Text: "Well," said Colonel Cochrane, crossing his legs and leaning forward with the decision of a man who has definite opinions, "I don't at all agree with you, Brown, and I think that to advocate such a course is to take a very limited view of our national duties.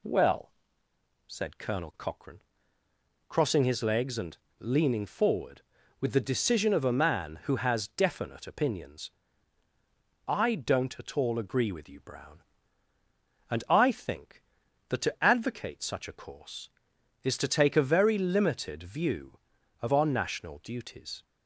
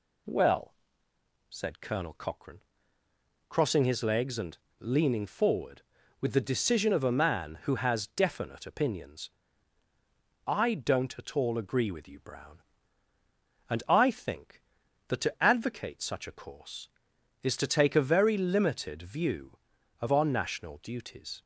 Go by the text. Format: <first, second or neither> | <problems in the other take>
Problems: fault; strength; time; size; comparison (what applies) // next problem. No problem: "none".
neither | pauses between "and" and "leaning"; slight; the same in both